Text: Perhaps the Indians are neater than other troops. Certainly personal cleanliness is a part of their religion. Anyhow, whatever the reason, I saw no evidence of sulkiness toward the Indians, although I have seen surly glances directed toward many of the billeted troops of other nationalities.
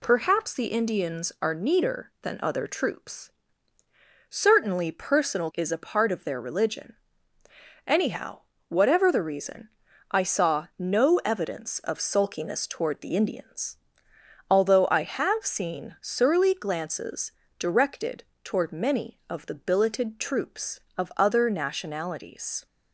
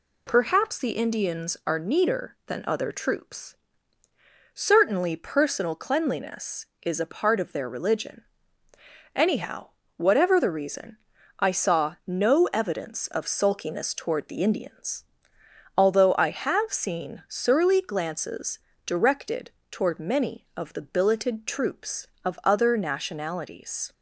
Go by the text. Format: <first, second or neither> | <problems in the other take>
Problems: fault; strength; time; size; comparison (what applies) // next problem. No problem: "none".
second | skips "cleanliness"; at 5.5 s // pauses between "glances" and "directed"; slight; at 17.3 s; 0.26 s long; slight in the second // pauses between "directed" and "toward"; slight; at 18.2 s; 0.20 s long; slight in the second